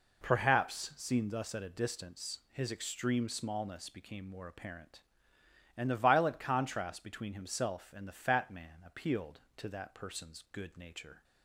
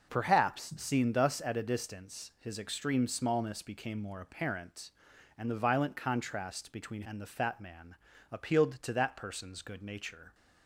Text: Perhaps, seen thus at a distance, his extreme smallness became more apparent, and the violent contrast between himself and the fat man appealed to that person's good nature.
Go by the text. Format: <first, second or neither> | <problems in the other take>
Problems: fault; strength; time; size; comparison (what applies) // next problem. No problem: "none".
first | skips "himself"; at 7.0 s // pauses between "man" and "appealed"; at 7.9 s; 0.38 s long